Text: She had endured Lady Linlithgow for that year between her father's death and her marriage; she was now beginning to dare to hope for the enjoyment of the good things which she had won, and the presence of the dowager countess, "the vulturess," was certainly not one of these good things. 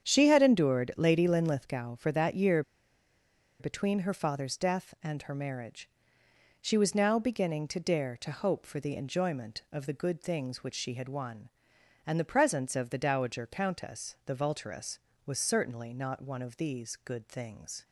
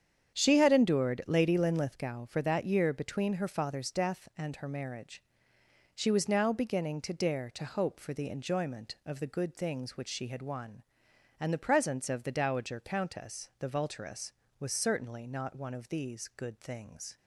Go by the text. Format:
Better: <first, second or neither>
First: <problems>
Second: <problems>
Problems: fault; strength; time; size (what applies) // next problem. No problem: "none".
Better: second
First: starts louder than the rest; strong; until 1.1 s; 8.5 dB // pauses between "year" and "between"; at 2.6 s; 0.98 s long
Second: starts louder than the rest; strong; until 1.4 s; 8.5 dB